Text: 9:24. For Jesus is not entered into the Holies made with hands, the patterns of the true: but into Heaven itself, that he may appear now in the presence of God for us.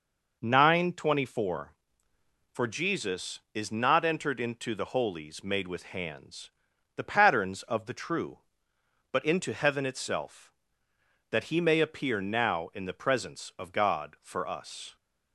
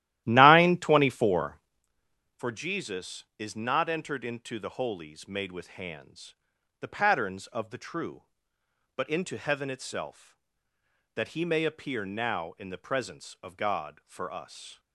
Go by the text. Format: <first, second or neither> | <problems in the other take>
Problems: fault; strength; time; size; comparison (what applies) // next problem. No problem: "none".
first | starts louder than the rest; strong; until 1.9 s; 14 dB